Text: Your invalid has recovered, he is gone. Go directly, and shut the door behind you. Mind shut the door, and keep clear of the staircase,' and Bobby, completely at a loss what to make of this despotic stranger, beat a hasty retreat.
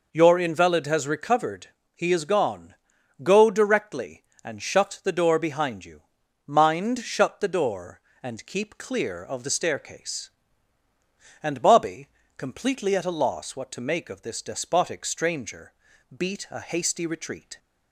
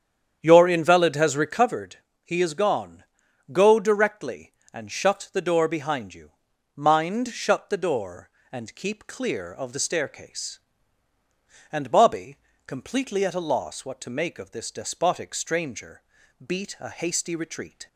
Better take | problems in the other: first | starts louder than the rest; strong; until 1.7 s; 8.5 dB

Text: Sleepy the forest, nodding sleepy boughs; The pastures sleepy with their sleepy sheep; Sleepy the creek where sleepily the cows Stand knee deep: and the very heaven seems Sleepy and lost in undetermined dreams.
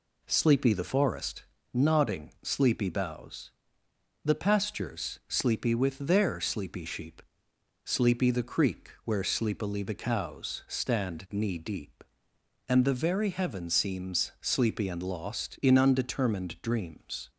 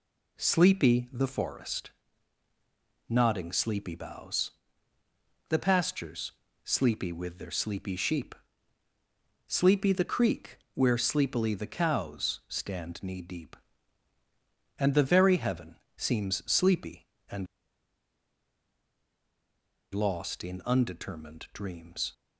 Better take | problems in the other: first | pauses between "pastures" and "sleepy"; slight; at 6.3 s; 0.32 s long // pauses between "creek" and "where"; slight; at 10.5 s; 0.16 s long // pauses between "heaven" and "seems"; slight; at 15.7 s; 0.18 s long // pauses between "and" and "lost"; strong; at 17.4 s; 2.4 s long

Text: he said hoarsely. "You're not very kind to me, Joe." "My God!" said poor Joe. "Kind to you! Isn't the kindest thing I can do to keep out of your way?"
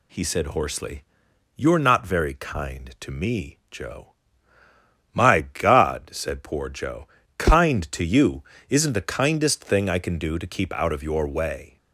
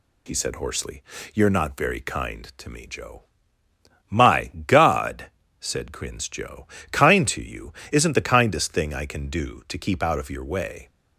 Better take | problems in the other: first | pauses between "My" and "God"; slight; at 4.5 s; 0.16 s long // says "crins" for "poor"; at 5.9 s

